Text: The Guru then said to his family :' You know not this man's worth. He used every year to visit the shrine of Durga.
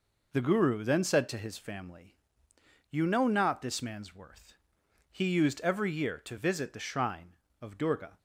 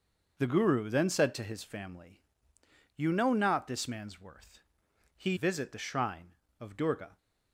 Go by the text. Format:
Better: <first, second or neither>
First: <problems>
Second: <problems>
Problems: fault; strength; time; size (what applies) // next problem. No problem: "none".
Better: first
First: none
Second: starts louder than the rest; until 1.3 s; 6 dB // skips "used every year to"; at 5.3 s